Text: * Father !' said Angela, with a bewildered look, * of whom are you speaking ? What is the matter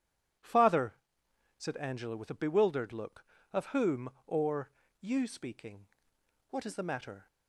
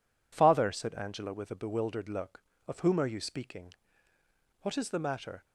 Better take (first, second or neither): second